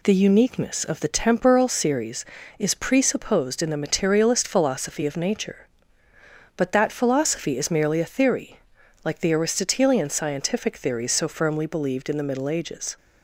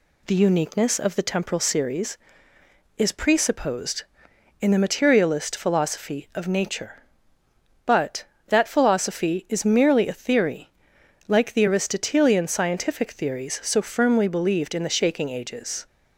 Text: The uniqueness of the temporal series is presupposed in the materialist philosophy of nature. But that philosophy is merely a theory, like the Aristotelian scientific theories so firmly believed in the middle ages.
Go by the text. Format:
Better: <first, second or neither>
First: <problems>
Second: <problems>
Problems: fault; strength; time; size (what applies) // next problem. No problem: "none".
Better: first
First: none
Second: says "shaking" for "middle"; at 14.9 s